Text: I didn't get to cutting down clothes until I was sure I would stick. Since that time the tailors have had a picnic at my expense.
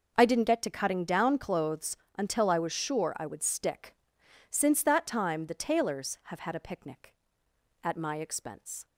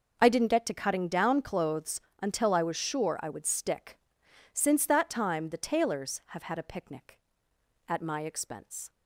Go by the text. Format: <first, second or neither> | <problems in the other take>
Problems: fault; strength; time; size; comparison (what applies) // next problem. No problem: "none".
neither | pauses between "clothes" and "until"; slight; the same in both